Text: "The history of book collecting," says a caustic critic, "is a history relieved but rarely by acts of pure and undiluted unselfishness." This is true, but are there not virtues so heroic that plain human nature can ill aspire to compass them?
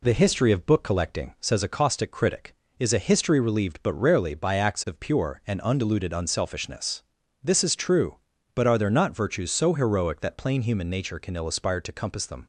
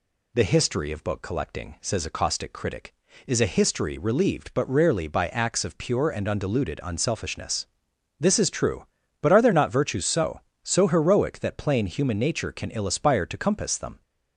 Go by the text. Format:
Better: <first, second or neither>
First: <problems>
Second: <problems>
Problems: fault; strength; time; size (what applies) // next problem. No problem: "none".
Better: first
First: none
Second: says "so" twice; at 10.6 s